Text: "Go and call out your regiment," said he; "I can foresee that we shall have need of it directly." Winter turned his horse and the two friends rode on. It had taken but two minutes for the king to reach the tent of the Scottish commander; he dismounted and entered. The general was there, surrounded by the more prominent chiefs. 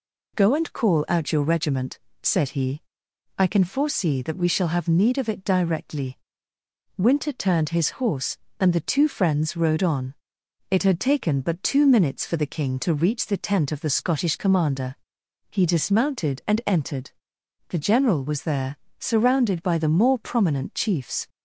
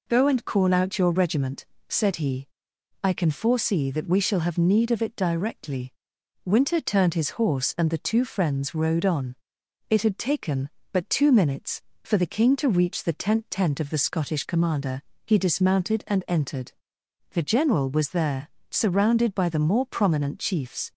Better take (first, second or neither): first